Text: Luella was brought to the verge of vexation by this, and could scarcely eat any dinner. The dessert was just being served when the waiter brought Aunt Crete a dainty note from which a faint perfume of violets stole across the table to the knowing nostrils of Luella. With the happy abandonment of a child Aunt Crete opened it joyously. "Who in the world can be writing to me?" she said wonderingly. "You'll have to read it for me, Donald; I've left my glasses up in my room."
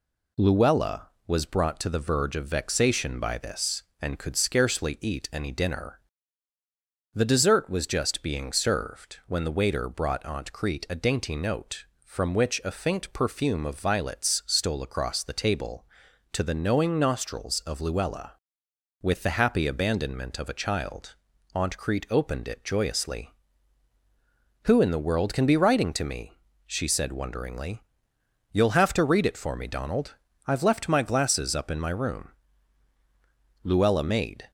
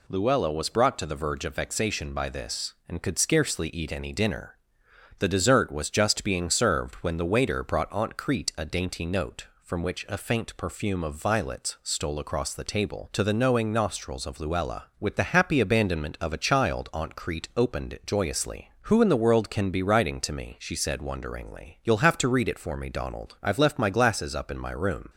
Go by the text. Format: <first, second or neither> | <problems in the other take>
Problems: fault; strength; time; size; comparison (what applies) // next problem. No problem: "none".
second | pauses between "child" and "Aunt"; at 21.1 s; 0.40 s long // goes on to say "Luella made"; noticeable; from 33.6 s on; 0.88 s long